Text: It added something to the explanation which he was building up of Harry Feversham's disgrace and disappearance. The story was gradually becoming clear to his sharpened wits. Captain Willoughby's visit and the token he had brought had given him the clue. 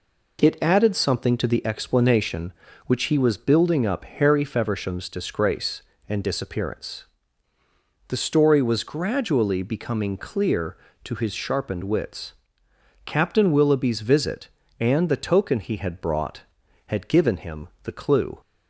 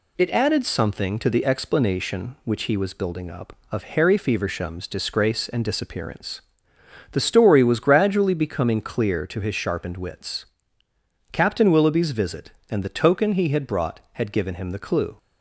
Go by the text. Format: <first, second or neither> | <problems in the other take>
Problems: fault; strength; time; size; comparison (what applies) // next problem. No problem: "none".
second | skips "of"; at 4.0 s // pauses between "him" and "the"; slight; at 17.6 s; 0.16 s long